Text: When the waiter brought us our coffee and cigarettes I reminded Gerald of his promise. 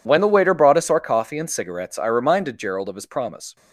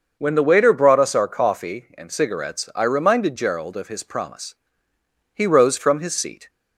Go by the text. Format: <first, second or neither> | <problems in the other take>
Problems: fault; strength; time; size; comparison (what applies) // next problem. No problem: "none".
first | starts louder than the rest; until 1.2 s; 6.5 dB // goes on to say "He rose from his seat"; noticeable; from 5.3 s on; 1.1 s long